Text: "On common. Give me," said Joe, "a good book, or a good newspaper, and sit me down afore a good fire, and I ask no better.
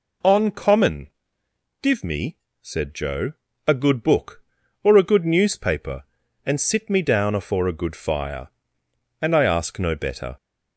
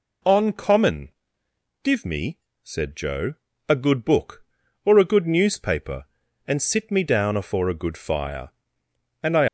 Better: first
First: none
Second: stops before "ask no better"; at 9.4 s

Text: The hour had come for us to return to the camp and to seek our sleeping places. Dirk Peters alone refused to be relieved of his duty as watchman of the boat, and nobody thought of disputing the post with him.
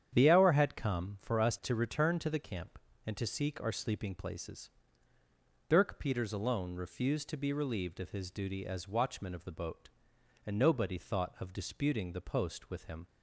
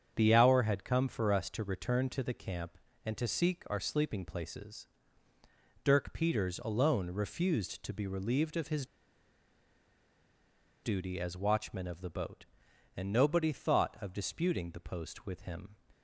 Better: first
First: starts louder than the rest; strong; until 1.1 s; 9 dB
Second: starts louder than the rest; strong; until 1.1 s; 7.5 dB // pauses between "his" and "duty"; strong; at 8.8 s; 1.9 s long

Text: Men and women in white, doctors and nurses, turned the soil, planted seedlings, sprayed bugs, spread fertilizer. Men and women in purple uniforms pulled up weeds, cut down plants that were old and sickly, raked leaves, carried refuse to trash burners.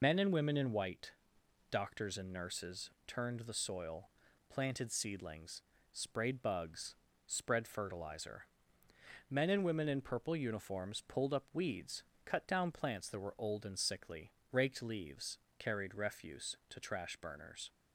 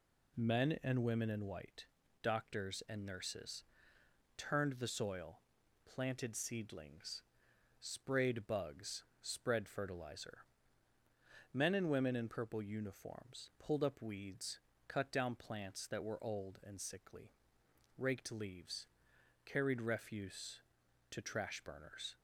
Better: second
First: loses the start of "Men"; at 0.0 s; 105 ms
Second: none

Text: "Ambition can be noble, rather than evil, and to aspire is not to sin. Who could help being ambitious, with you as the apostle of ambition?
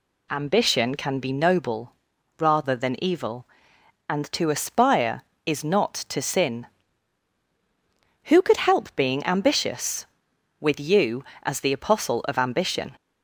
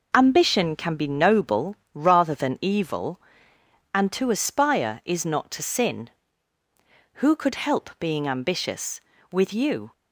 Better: first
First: none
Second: stops before "as the apostle of ambition"; at 9.9 s

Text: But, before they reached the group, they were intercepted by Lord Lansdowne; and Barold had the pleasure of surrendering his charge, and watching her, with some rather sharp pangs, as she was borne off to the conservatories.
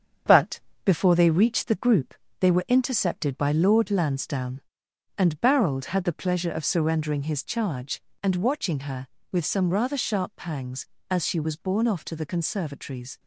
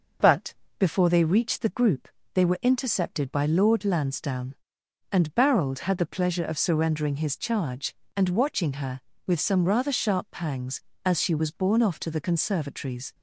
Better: second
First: gets quieter; noticeable; throughout; 6 dB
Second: none

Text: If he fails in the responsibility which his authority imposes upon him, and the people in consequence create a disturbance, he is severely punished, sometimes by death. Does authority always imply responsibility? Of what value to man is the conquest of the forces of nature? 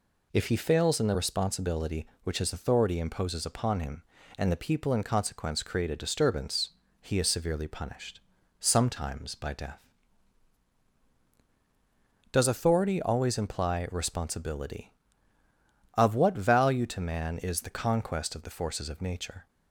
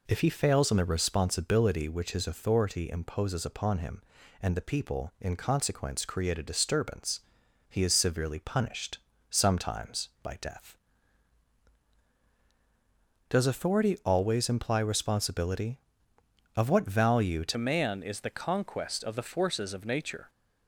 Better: first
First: none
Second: changes voice at "man"; from 17.5 s on; 2.7 s long

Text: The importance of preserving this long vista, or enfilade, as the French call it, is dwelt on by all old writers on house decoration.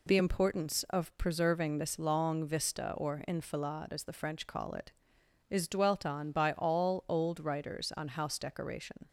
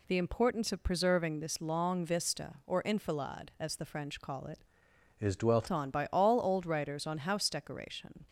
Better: first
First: none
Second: changes voice from "is" to "dwelt"; from 5.2 to 5.6 s; 0.4 s long

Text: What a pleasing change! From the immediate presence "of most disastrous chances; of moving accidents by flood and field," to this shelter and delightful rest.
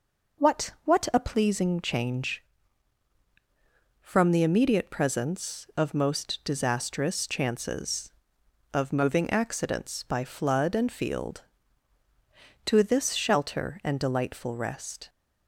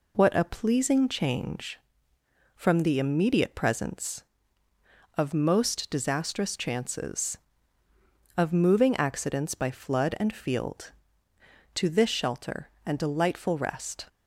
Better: second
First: says "What" twice; at 0.8 s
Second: none

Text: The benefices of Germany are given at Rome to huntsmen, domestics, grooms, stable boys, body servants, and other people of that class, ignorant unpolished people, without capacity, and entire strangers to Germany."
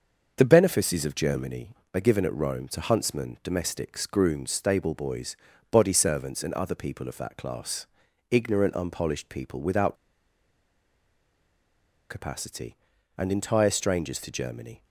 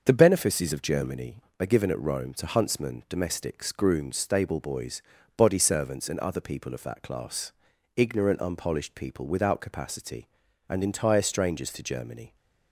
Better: second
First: starts louder than the rest; until 1.3 s; 6.5 dB // pauses between "without" and "capacity"; strong; at 9.9 s; 2.1 s long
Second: starts louder than the rest; until 1.0 s; 6.5 dB

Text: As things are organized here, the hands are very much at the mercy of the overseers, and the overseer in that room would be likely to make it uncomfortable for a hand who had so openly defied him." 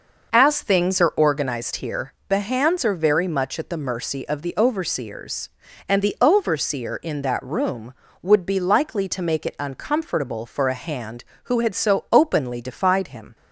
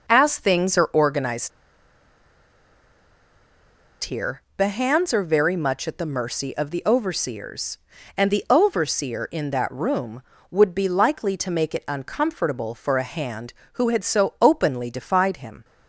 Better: first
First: none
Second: pauses between "organized" and "here"; strong; at 1.5 s; 2.5 s long

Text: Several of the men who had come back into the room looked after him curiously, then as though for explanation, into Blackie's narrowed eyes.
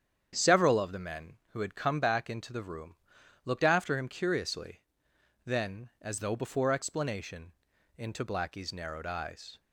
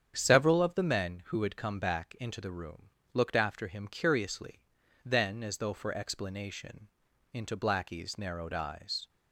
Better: second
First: starts louder than the rest; strong; until 1.3 s; 8.5 dB // pauses between "room" and "looked"; noticeable; at 2.9 s; 0.48 s long // says "before" for "for"; at 6.3 s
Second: starts louder than the rest; strong; until 1.1 s; 8.5 dB // pauses between "room" and "looked"; slight; at 2.8 s; 0.24 s long

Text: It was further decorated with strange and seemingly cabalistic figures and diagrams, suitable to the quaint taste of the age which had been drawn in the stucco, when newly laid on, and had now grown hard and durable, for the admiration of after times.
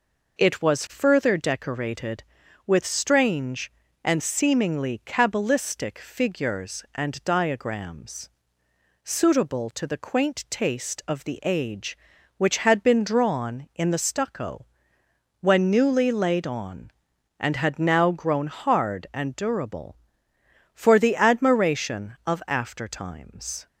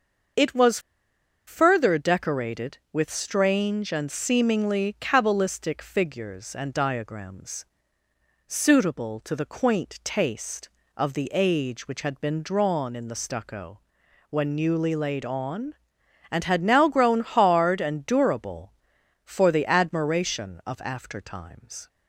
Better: first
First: none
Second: starts louder than the rest; until 2.0 s; 6.5 dB // pauses between "was" and "further"; noticeable; at 0.7 s; 0.68 s long

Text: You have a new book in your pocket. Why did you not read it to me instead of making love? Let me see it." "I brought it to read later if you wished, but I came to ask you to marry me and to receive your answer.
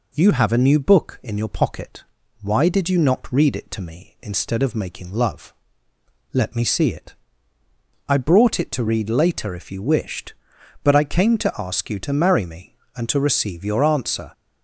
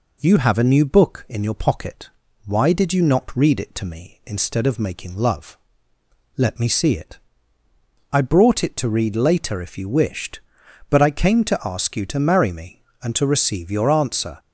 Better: neither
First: none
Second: none

